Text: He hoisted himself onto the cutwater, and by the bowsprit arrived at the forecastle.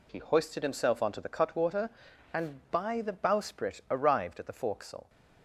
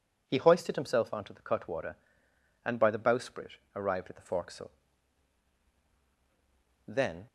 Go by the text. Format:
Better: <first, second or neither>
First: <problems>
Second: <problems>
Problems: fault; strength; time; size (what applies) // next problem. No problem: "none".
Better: first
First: none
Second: pauses between "bowsprit" and "arrived"; slight; at 3.5 s; 0.20 s long // goes on to say "Then"; slight; from 6.8 s on; 0.38 s long